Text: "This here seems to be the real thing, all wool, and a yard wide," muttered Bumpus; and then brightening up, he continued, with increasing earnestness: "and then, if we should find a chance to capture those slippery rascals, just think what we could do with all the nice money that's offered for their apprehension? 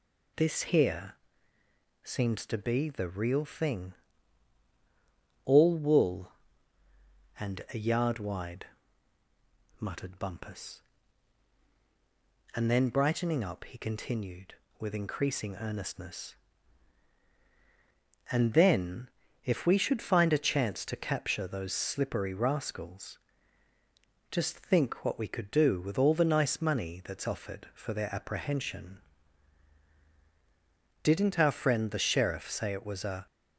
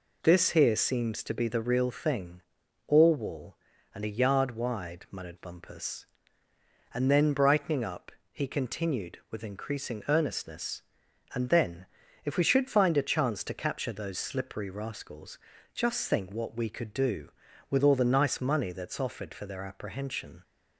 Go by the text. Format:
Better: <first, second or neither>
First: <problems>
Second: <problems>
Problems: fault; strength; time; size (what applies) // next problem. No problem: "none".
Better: second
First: pauses between "here" and "seems"; noticeable; at 1.1 s; 0.88 s long // goes on to say "Didn't our friend the sheriff say it was a"; strong; from 31.0 s on; 2.2 s long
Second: none